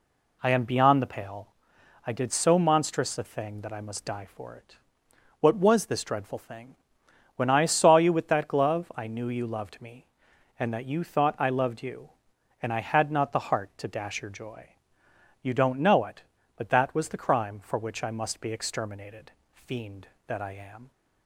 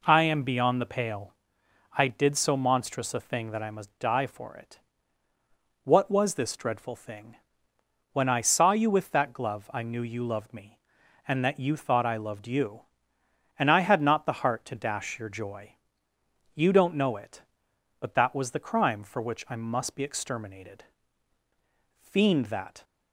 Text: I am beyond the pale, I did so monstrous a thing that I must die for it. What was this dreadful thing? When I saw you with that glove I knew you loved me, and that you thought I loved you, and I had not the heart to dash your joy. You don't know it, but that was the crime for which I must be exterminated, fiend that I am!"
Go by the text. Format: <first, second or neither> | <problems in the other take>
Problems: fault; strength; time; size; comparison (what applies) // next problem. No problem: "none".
first | stops before "I am"; at 22.8 s